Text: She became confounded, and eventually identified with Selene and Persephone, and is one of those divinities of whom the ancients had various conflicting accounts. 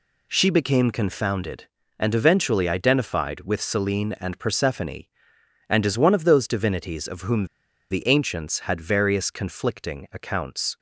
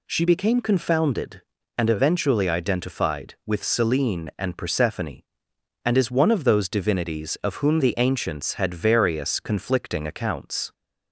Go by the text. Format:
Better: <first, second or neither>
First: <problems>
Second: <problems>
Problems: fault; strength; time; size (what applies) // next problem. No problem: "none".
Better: second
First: pauses between "whom" and "the"; at 7.4 s; 0.43 s long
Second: none